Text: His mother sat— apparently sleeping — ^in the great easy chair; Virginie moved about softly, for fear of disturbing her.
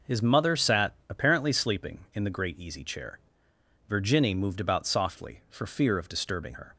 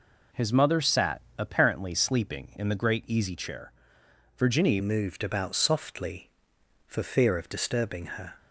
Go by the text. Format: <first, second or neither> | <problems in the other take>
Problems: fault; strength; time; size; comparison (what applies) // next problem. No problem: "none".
first | changes voice at "moved"; from 4.8 s on; 3.5 s long